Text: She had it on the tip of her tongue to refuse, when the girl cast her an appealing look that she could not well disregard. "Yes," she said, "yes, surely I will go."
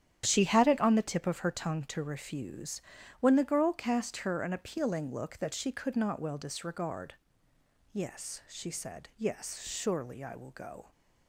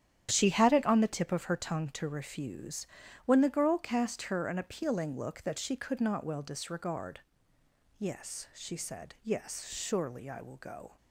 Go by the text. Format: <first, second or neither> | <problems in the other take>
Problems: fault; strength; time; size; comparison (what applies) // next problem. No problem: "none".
neither | starts louder than the rest; strong; the same in both